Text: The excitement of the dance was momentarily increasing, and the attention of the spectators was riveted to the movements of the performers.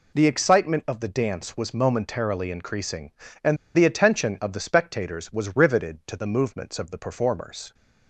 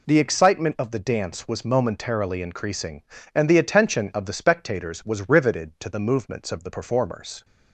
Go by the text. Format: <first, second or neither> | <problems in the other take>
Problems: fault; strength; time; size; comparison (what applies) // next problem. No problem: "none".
second | pauses between "and" and "the"; slight; at 3.5 s; 0.19 s long